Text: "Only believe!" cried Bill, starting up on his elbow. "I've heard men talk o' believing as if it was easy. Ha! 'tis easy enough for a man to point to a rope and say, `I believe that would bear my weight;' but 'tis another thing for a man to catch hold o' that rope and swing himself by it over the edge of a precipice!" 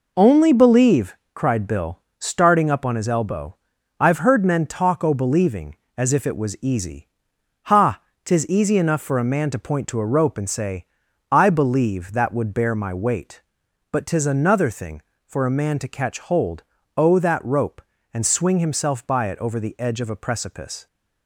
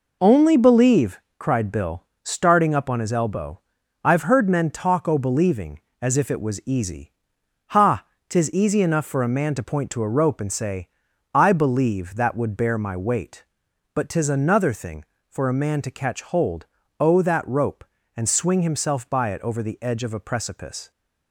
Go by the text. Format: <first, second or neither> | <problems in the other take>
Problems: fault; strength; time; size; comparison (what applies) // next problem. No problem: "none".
neither | pauses between "hold" and "o"; slight; the same in both